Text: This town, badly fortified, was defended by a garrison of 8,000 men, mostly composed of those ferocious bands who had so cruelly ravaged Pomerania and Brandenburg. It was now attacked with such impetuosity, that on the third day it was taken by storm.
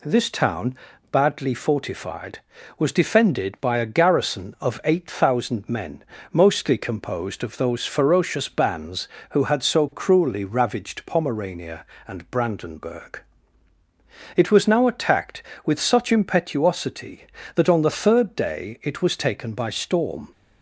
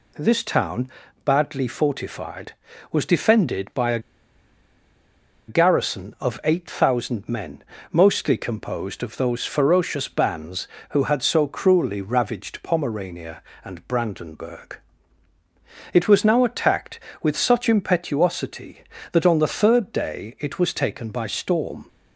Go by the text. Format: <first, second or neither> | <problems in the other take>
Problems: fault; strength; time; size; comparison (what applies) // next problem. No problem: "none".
first | pauses between "a" and "garrison"; strong; at 3.9 s; 1.4 s long